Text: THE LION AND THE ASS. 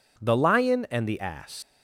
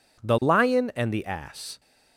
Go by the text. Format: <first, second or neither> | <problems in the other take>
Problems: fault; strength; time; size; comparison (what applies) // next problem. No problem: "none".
second | leaves "ASS" unfinished; at 1.6 s; 110 ms